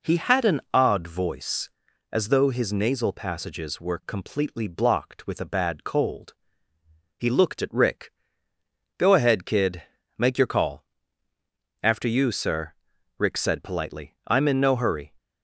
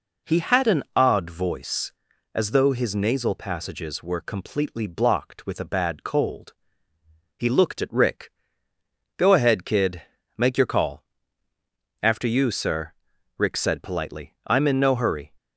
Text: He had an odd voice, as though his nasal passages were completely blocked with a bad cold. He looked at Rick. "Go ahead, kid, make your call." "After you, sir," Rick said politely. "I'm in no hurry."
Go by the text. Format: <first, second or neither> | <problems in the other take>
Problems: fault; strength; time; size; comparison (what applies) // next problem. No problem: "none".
neither | none